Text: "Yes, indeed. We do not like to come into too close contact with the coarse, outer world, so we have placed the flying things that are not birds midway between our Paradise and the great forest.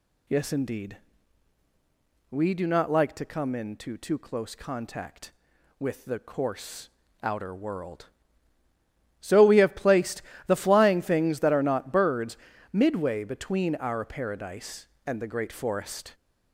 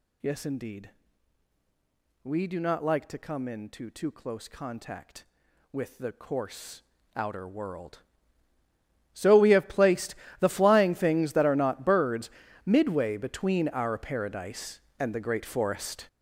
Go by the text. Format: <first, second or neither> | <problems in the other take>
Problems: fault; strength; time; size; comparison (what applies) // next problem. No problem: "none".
first | gets louder; strong; throughout; 11 dB // pauses between "placed" and "the"; slight; at 10.1 s; 0.26 s long; slight in the first // pauses between "birds" and "midway"; slight; at 12.2 s; 0.36 s long; slight in the first